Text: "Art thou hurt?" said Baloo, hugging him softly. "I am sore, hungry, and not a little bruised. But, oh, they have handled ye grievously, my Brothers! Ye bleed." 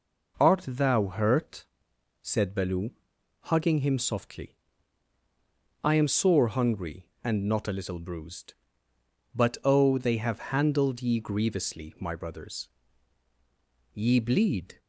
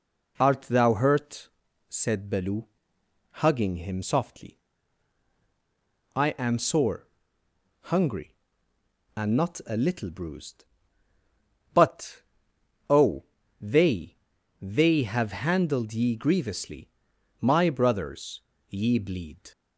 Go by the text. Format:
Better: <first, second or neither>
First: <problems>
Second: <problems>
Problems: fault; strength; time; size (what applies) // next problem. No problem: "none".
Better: first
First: none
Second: says "they" twice; at 14.5 s